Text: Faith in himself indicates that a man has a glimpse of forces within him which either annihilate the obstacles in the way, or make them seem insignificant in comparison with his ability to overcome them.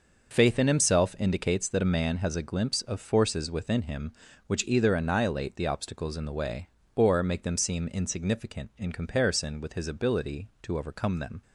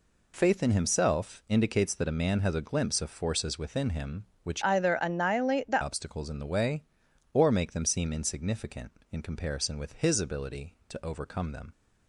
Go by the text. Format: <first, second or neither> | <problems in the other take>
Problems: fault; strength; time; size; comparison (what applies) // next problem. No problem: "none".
first | changes voice from "either" to "the"; from 4.6 to 5.8 s; 1.2 s long